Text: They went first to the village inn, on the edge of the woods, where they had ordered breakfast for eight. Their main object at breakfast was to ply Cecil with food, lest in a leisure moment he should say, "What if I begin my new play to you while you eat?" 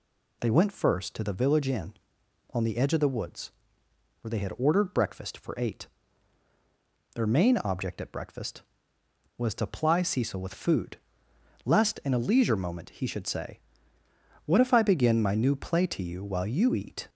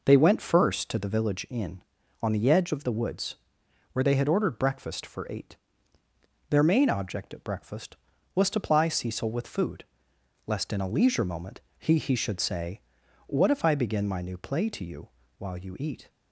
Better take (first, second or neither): first